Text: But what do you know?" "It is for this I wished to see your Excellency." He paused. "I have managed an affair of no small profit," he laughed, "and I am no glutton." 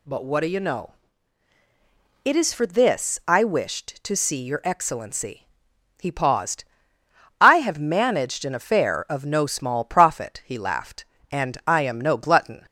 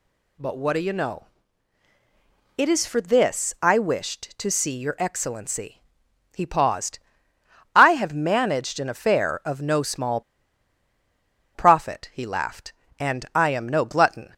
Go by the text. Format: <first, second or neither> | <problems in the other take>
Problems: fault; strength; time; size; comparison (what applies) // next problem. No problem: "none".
first | pauses between "small" and "profit"; strong; at 10.2 s; 1.3 s long